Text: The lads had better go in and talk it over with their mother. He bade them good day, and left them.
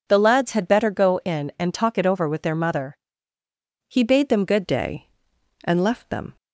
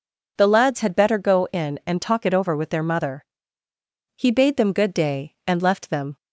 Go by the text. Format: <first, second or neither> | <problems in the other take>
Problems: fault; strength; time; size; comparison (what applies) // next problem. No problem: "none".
second | changes voice at "day"; from 4.6 s on; 1.7 s long